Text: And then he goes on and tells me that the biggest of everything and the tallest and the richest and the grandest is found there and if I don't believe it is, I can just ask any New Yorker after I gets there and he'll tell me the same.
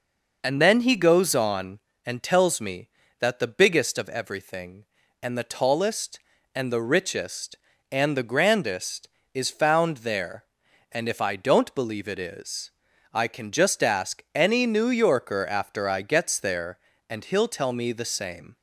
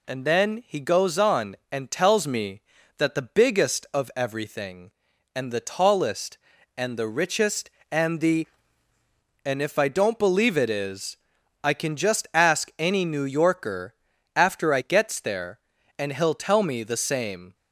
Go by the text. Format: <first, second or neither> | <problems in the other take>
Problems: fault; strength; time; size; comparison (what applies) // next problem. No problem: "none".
first | skips "grandest is found there"; at 8.9 s // pauses between "Yorker" and "after"; at 13.9 s; 0.44 s long